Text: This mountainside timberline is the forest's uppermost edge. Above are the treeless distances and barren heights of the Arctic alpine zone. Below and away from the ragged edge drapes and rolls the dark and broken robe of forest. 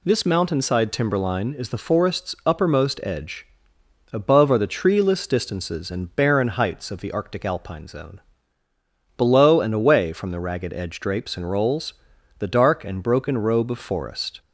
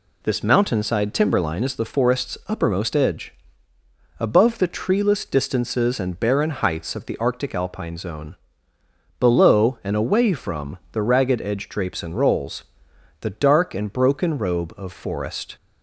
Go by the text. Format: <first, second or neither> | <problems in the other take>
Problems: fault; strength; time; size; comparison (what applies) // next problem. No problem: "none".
first | skips "are"; at 4.5 s // pauses between "rolls" and "the"; noticeable; at 12.6 s; 0.58 s long; noticeable in the first